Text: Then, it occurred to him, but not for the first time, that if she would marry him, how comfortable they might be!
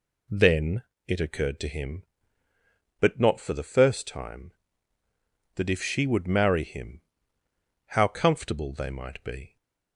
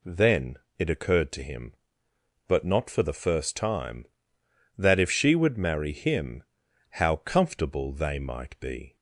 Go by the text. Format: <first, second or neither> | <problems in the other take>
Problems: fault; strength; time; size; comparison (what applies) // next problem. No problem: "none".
neither | none